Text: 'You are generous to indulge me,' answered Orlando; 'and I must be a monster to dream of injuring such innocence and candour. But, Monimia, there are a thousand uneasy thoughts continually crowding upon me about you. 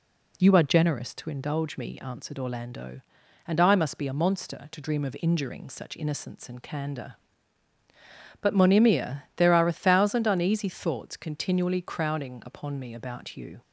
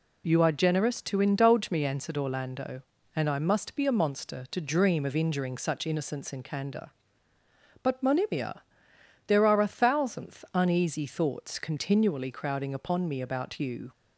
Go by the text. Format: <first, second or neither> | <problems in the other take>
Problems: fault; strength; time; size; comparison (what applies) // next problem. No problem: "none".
first | says "thousandth" for "thousand"; at 9.6 s